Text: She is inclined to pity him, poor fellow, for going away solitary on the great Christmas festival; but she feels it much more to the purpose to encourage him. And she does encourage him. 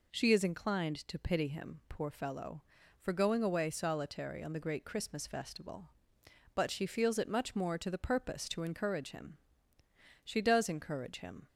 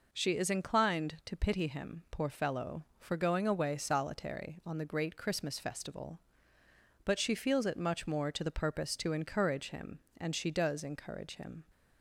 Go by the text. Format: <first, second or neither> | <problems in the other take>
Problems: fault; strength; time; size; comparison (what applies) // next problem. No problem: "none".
second | skips "And"; at 9.8 s